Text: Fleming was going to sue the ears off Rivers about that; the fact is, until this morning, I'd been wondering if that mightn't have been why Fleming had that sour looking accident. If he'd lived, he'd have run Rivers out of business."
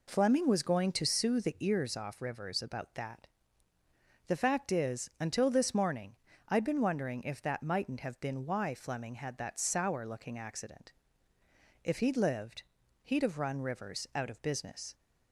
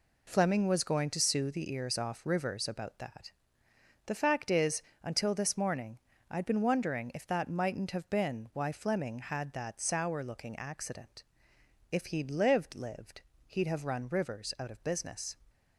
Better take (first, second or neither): first